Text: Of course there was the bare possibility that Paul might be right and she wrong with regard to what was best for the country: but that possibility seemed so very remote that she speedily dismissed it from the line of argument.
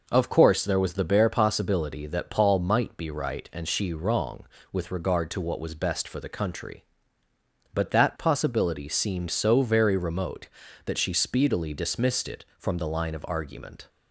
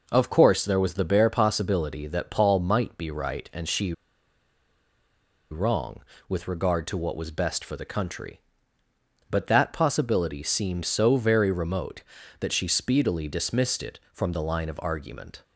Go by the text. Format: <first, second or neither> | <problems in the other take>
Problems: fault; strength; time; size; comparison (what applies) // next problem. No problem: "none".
first | pauses between "she" and "wrong"; strong; at 3.9 s; 1.5 s long